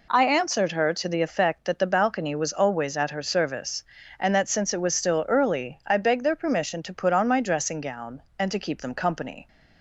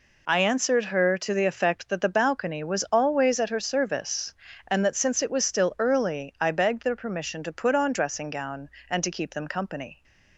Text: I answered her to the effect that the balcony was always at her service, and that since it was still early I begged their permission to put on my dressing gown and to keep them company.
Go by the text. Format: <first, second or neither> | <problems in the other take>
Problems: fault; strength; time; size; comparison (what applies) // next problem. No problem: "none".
first | skips "my"; at 7.9 s